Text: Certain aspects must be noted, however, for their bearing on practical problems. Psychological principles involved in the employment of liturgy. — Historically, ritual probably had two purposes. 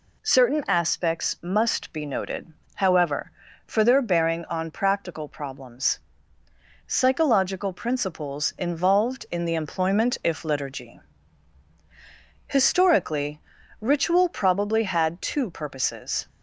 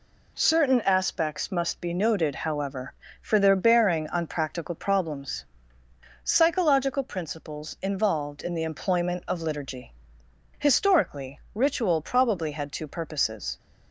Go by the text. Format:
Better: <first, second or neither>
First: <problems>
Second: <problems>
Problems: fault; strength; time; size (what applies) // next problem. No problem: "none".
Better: second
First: says "if" for "of"; at 10.2 s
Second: none